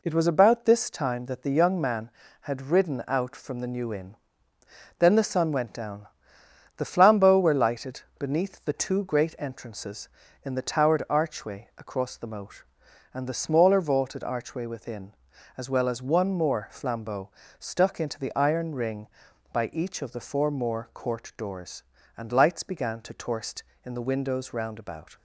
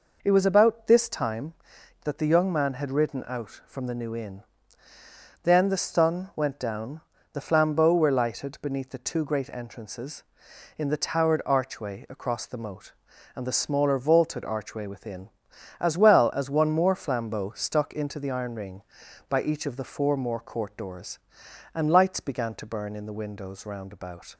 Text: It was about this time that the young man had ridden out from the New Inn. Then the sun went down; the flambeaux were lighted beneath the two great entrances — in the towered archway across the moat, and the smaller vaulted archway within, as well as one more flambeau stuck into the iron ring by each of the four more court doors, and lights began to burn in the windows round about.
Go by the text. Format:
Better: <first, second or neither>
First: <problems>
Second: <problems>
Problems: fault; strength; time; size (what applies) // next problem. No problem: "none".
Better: second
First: pauses between "lighted" and "beneath"; slight; at 8.0 s; 0.18 s long // pauses between "flambeau" and "stuck"; slight; at 17.2 s; 0.28 s long // says "torst" for "burn"; at 23.1 s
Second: none